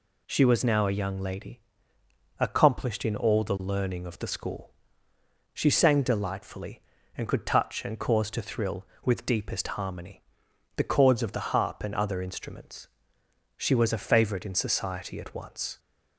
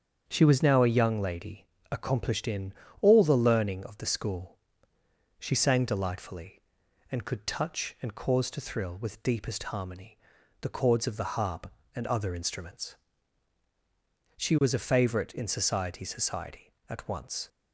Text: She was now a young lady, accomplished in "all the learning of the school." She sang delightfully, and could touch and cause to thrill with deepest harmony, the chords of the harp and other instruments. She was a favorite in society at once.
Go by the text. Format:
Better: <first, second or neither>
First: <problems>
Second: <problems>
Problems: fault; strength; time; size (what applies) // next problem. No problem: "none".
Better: first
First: none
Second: starts louder than the rest; strong; until 1.2 s; 7.5 dB // pauses between "in" and "all"; slight; at 2.7 s; 0.26 s long // says "society" twice; at 16.0 s